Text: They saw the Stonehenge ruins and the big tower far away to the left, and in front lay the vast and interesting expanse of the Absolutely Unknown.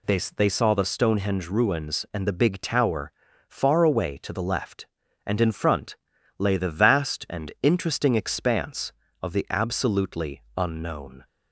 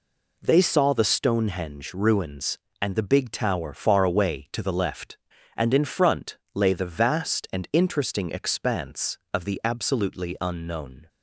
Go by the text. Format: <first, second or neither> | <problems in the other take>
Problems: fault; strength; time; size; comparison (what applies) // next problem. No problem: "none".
second | says "They" twice; at 0.3 s // pauses between "tower" and "far"; at 3.1 s; 0.38 s long // pauses between "front" and "lay"; at 5.9 s; 0.40 s long; slight in the second